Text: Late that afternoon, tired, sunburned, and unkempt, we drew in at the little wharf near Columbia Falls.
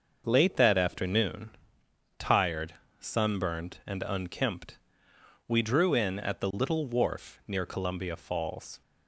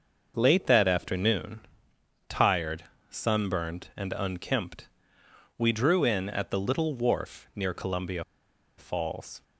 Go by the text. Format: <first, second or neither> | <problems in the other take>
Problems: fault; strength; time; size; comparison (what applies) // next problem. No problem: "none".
first | starts louder than the rest; until 1.3 s; 6 dB; also in the first // pauses between "Columbia" and "Falls"; noticeable; at 8.2 s; 0.55 s long